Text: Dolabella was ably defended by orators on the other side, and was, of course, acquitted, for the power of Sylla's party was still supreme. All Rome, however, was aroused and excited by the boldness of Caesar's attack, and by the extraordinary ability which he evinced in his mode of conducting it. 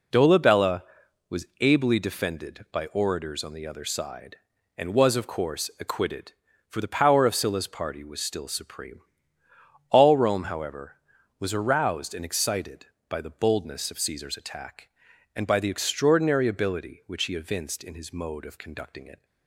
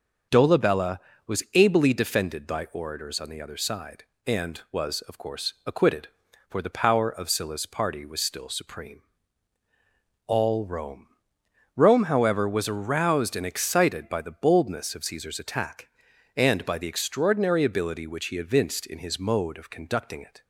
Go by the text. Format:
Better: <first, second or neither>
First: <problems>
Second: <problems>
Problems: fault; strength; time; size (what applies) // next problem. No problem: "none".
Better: first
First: none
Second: starts louder than the rest; until 1.6 s; 6.5 dB // says "Rome" twice; at 11.7 s